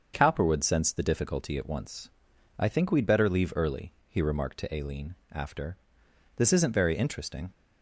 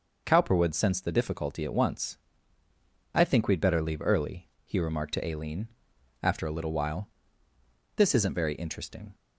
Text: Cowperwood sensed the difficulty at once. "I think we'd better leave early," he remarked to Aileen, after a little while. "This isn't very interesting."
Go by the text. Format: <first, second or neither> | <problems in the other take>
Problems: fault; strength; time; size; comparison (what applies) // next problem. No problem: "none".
second | starts louder than the rest; until 1.1 s; 7 dB // skips "a little while"; at 6.0 s